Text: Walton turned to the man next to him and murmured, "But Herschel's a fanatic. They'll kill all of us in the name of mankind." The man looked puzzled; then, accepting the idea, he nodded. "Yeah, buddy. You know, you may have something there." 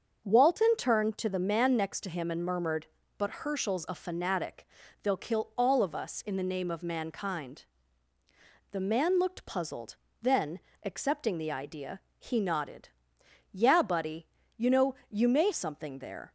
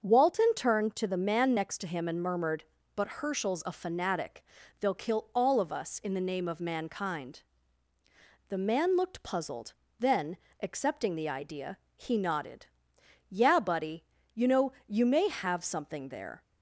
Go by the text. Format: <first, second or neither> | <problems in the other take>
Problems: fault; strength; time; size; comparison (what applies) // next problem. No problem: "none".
second | starts louder than the rest; until 1.2 s; 7 dB; also in the second // skips "have"; at 15.5 s